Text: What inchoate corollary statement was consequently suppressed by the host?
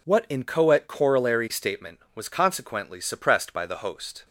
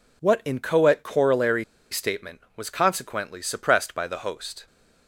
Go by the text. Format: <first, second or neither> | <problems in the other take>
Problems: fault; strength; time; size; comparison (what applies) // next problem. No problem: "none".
first | pauses between "corollary" and "statement"; slight; at 1.6 s; 0.27 s long